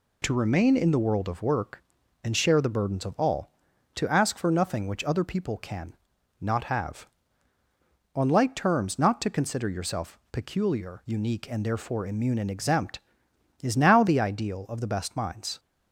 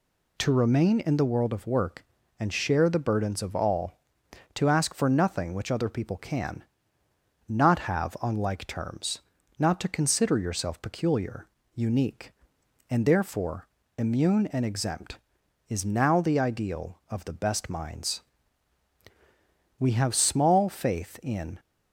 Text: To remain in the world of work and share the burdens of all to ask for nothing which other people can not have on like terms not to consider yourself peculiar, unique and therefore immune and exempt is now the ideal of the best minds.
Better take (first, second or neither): first